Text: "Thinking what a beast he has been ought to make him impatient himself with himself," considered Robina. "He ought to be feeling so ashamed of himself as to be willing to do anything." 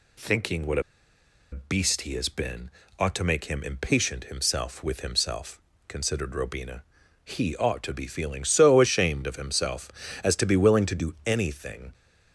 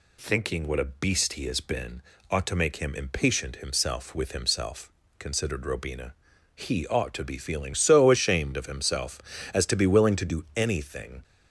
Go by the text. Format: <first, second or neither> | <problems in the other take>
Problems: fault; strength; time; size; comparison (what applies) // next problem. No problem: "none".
second | pauses between "what" and "a"; noticeable; at 0.8 s; 0.71 s long // pauses between "been" and "ought"; slight; at 2.6 s; 0.28 s long; slight in the second